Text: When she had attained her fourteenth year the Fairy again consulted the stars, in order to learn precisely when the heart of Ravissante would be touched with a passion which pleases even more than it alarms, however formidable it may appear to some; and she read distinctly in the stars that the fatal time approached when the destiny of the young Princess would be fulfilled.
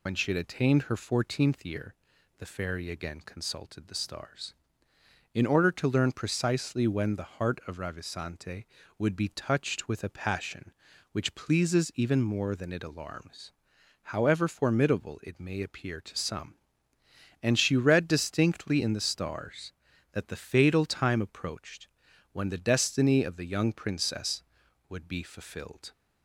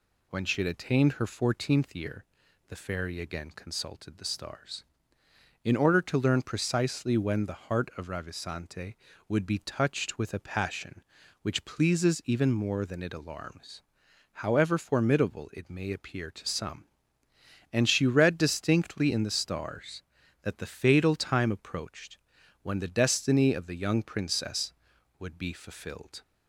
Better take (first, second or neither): second